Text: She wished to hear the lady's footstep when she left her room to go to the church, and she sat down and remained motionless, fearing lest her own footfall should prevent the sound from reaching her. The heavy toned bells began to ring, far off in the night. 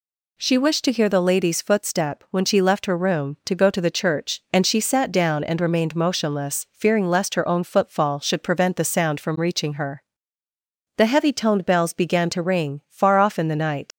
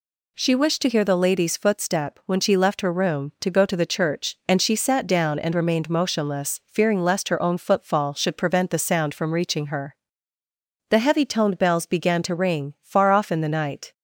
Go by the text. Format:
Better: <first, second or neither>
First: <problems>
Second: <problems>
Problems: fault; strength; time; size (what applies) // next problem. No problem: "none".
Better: second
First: leaves "night" unfinished; at 13.9 s; 95 ms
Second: none